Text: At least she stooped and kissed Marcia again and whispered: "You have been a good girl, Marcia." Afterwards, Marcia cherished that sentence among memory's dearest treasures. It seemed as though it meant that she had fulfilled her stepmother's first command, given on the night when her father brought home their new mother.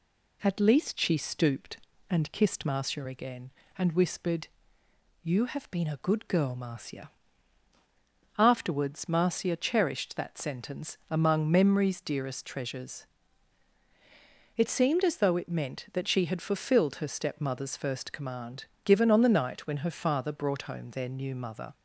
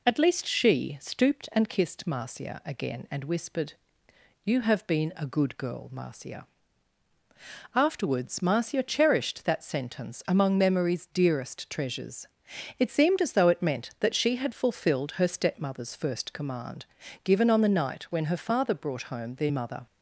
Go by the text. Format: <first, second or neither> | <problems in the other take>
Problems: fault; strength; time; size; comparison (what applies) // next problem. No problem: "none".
first | skips "new"; at 19.5 s